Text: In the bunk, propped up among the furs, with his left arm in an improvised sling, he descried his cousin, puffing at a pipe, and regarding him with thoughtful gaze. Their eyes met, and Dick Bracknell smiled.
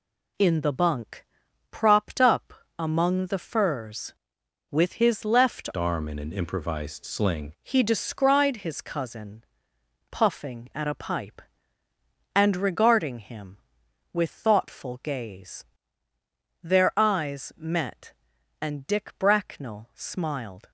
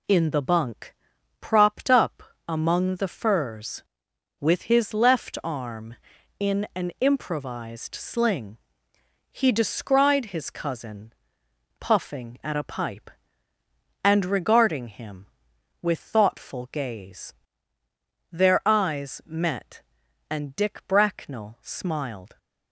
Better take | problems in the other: second | pauses between "up" and "among"; slight; at 2.5 s; 0.24 s long; slight in the second // changes voice from "arm" to "sling"; from 5.7 to 7.5 s; 1.8 s long

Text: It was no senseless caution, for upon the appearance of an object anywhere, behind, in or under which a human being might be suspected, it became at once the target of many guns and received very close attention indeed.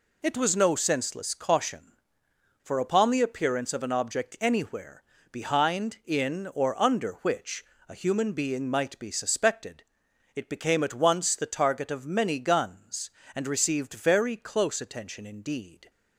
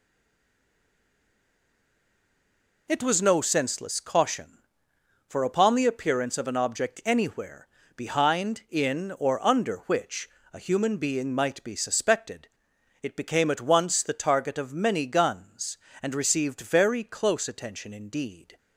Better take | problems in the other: first | stays silent before the first word; strong; until 2.8 s; 2.8 s long // pauses between "which" and "a"; slight; at 10.2 s; 0.24 s long; slight in the first

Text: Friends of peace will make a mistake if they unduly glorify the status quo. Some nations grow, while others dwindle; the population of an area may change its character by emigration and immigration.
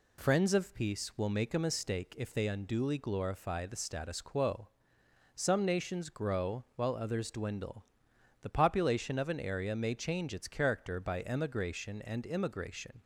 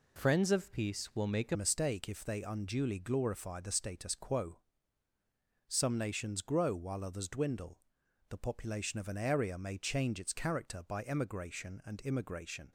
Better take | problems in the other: first | changes voice at "mistake"; from 1.5 s on; 11.2 s long

